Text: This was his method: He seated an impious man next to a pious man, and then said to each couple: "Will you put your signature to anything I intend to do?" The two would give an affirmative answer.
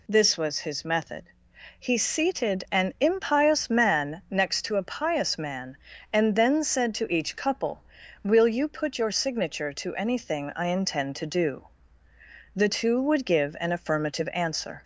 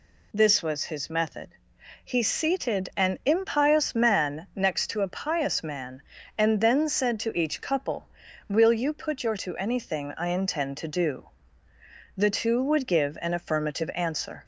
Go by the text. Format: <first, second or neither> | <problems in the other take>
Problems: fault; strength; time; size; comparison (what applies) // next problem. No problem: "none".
first | skips "signature"; at 9.3 s